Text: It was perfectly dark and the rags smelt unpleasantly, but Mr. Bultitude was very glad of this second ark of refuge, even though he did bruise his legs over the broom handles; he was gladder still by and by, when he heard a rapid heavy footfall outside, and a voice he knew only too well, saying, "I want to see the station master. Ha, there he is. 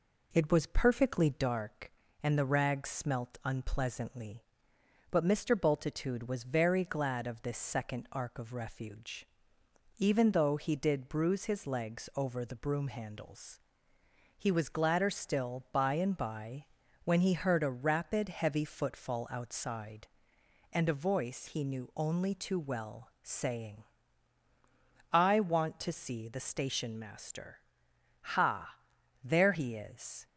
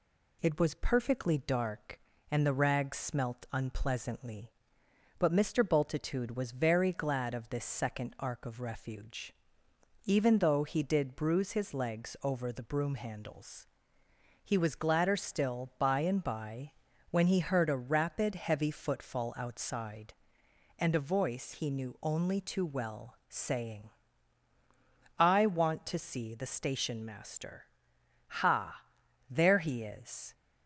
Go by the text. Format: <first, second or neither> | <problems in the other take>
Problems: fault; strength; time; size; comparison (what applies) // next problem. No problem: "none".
second | starts louder than the rest; noticeable; until 1.5 s; 4 dB